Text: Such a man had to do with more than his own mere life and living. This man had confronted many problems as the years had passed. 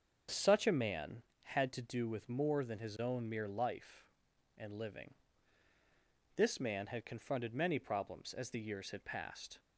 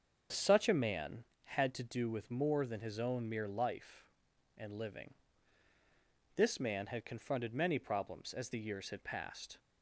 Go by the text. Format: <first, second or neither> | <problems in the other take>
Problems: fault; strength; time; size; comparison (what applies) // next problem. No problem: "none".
neither | starts louder than the rest; the same in both